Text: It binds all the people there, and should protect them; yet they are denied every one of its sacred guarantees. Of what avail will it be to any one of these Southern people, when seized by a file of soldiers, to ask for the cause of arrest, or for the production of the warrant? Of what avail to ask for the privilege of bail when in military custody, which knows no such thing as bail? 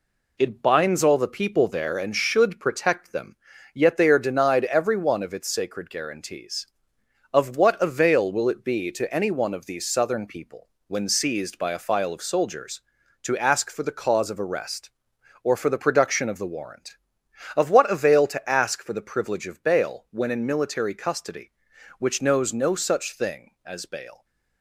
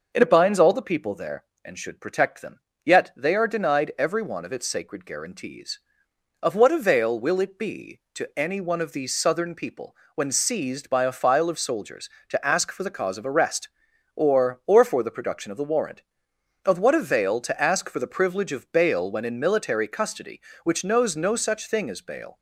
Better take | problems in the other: first | says "or" twice; at 14.6 s

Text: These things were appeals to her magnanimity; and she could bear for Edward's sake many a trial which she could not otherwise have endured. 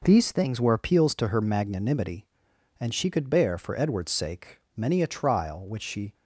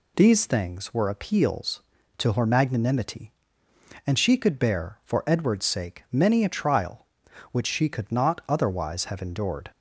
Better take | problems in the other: second | pauses between "sake" and "many"; slight; at 4.5 s; 0.16 s long // stops before "could not otherwise have endured"; at 6.1 s

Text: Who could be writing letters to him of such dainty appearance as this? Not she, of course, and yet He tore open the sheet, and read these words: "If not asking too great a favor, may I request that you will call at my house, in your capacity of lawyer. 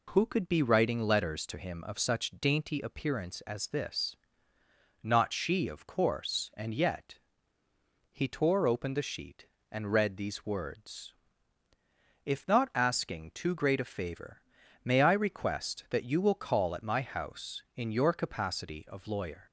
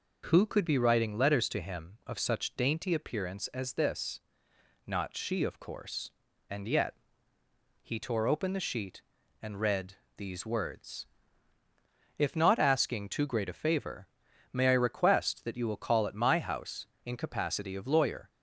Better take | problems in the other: first | pauses between "yet" and "He"; noticeable; at 6.9 s; 0.88 s long; noticeable in the first // pauses between "read" and "these"; slight; at 9.9 s; 0.20 s long // skips "your"; at 17.1 s

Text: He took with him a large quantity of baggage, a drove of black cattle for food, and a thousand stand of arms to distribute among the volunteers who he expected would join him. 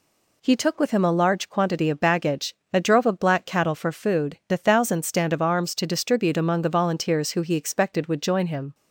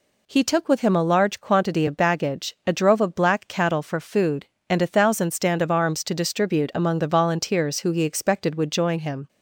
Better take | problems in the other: second | skips "and"; at 4.4 s

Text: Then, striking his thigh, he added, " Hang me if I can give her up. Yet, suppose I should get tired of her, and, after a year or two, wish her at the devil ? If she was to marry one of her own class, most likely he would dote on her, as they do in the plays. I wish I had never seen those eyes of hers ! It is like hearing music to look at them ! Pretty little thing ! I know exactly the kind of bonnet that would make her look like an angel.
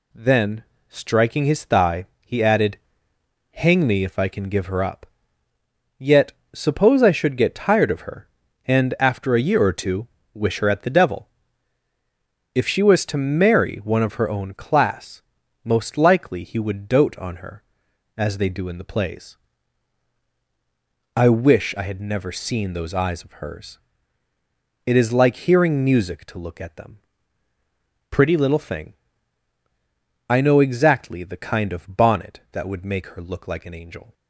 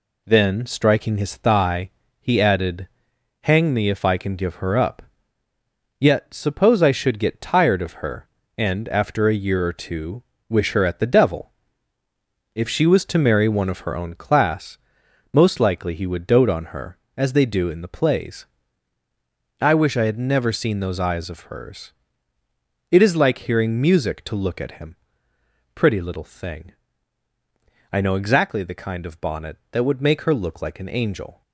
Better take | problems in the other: first | says "him" for "them"; at 24.7 s

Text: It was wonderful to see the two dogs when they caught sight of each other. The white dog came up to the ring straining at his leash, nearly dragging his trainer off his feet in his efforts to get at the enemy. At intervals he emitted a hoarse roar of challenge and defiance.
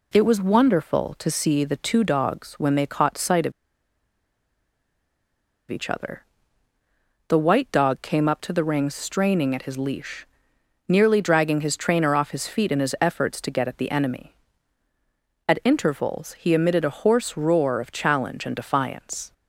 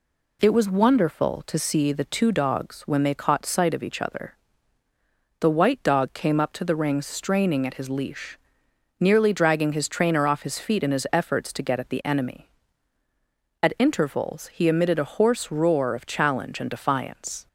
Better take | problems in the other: second | pauses between "of" and "each"; strong; at 3.5 s; 2.1 s long

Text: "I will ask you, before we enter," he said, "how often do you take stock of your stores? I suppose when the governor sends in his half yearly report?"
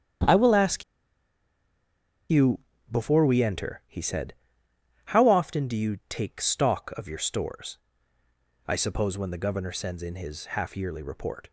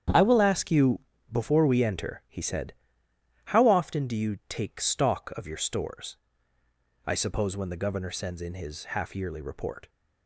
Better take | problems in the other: second | starts louder than the rest; strong; until 3.0 s; 9 dB; strong in the second // pauses between "ask" and "you"; strong; at 0.8 s; 1.4 s long

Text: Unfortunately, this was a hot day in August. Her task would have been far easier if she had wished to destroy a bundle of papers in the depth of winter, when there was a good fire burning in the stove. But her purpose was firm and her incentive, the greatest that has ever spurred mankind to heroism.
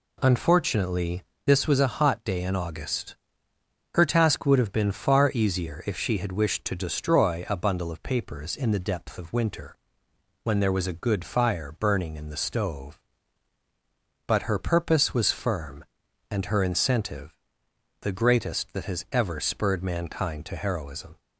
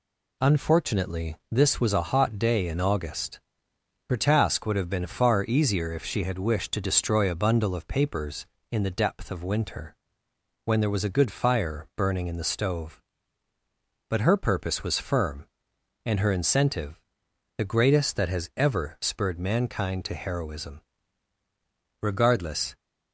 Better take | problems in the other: first | goes on to say "Regardless"; noticeable; from 22.0 s on; 0.74 s long

